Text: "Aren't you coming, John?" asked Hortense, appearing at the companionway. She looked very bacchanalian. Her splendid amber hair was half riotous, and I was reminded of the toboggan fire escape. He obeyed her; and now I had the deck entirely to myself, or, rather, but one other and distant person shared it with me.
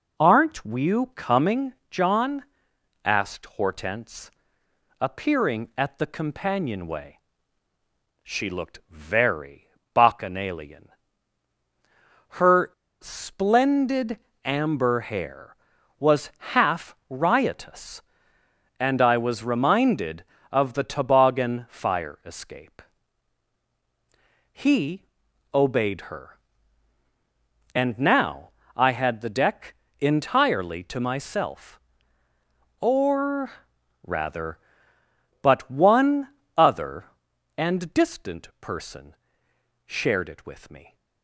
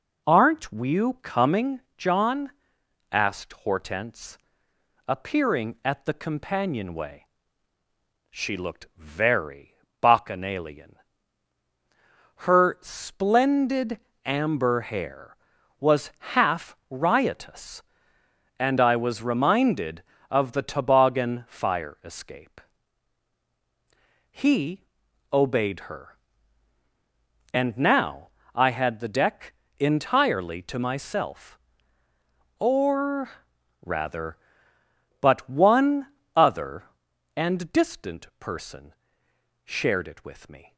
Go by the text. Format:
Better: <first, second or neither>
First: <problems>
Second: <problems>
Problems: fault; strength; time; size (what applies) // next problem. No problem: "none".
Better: second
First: pauses between "very" and "bacchanalian"; slight; at 9.6 s; 0.24 s long // pauses between "Her" and "splendid"; slight; at 12.7 s; 0.29 s long // pauses between "splendid" and "amber"; slight; at 14.1 s; 0.24 s long // pauses between "was" and "half"; slight; at 16.2 s; 0.22 s long // pauses between "He" and "obeyed"; noticeable; at 25.0 s; 0.48 s long // pauses between "now" and "I"; slight; at 28.4 s; 0.26 s long // pauses between "deck" and "entirely"; slight; at 29.7 s; 0.26 s long // pauses between "one" and "other"; slight; at 36.2 s; 0.30 s long // pauses between "person" and "shared"; noticeable; at 39.1 s; 0.70 s long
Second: pauses between "very" and "bacchanalian"; slight; at 9.7 s; 0.24 s long // pauses between "splendid" and "amber"; slight; at 13.9 s; 0.24 s long // pauses between "was" and "half"; slight; at 16.0 s; 0.22 s long // pauses between "He" and "obeyed"; noticeable; at 24.8 s; 0.48 s long // pauses between "now" and "I"; slight; at 28.2 s; 0.26 s long // pauses between "deck" and "entirely"; slight; at 29.5 s; 0.26 s long // pauses between "one" and "other"; slight; at 36.0 s; 0.30 s long // pauses between "person" and "shared"; noticeable; at 38.9 s; 0.70 s long